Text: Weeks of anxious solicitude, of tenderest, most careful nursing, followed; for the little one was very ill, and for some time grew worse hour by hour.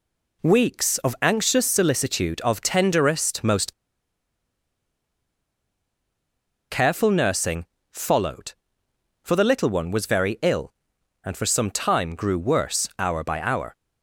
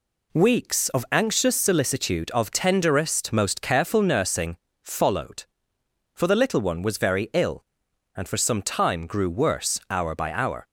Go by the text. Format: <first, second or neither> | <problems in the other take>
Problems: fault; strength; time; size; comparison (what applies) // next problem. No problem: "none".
second | pauses between "most" and "careful"; strong; at 3.7 s; 2.9 s long